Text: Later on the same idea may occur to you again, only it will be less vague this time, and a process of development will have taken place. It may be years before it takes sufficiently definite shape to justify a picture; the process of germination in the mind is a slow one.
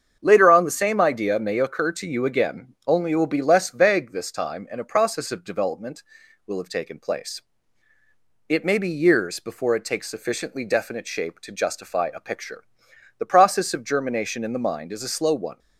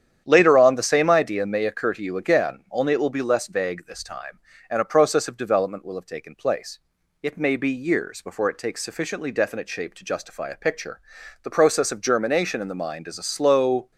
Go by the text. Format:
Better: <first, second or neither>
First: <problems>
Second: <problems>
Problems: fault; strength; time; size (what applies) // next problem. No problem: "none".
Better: first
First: starts louder than the rest; strong; until 1.2 s; 7.5 dB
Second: starts louder than the rest; strong; until 1.2 s; 9.5 dB // stops before "one"; at 13.9 s